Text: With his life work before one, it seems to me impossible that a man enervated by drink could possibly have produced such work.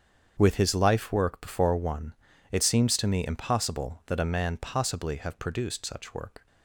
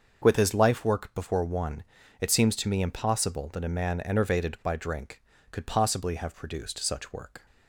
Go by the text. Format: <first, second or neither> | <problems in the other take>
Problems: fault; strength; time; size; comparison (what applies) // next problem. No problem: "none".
second | starts louder than the rest; strong; until 1.3 s; 7.5 dB; also in the second // skips "enervated by drink could"; at 4.5 s